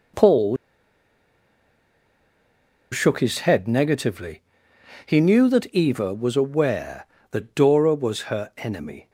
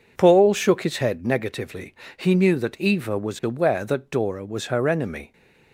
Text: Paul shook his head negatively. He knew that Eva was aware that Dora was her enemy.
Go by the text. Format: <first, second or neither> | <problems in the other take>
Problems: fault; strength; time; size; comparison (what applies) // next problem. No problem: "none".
second | pauses between "Paul" and "shook"; strong; at 0.5 s; 2.3 s long